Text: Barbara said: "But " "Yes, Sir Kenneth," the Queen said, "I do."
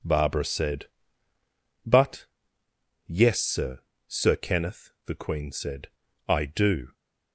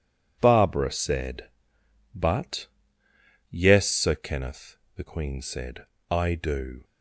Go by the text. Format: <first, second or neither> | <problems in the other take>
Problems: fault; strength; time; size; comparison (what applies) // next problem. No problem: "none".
second | says "Sir" twice; at 4.0 s